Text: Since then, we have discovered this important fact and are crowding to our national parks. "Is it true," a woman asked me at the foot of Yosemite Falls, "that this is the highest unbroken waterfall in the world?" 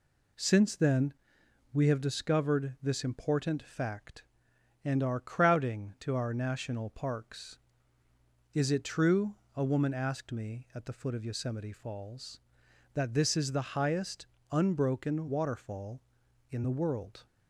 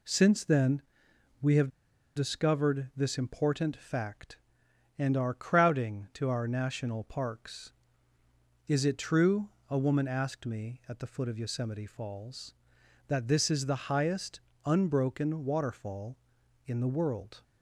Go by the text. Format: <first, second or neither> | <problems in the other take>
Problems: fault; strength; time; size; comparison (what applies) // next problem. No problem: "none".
first | pauses between "have" and "discovered"; noticeable; at 1.6 s; 0.46 s long // pauses between "highest" and "unbroken"; slight; at 14.4 s; 0.24 s long; slight in the first